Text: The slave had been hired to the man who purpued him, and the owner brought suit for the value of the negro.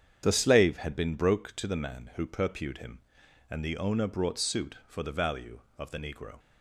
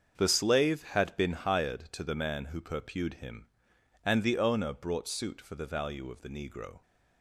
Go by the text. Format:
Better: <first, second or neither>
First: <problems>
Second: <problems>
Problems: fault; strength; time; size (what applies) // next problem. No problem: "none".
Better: second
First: starts louder than the rest; strong; until 1.2 s; 8 dB // says "broke" for "hired"; at 1.1 s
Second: starts louder than the rest; until 1.2 s; 7 dB